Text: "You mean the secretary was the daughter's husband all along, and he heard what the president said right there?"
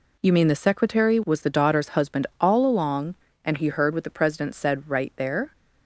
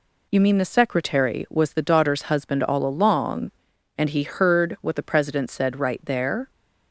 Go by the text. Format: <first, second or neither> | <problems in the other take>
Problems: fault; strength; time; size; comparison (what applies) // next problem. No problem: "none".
neither | none